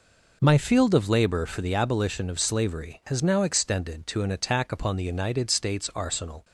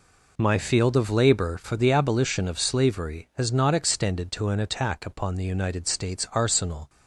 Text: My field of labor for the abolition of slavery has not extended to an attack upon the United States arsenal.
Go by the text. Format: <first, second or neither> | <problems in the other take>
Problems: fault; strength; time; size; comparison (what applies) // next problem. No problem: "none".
second | says "now" for "not"; at 3.2 s